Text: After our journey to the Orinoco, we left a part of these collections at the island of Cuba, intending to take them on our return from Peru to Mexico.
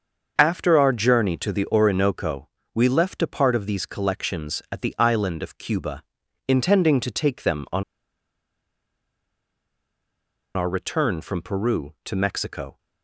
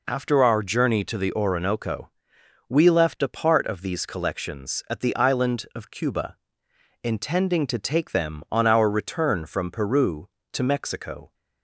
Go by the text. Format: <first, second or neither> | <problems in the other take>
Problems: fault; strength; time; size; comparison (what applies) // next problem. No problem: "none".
second | starts louder than the rest; until 1.3 s; 6.5 dB // pauses between "on" and "our"; strong; at 7.8 s; 2.7 s long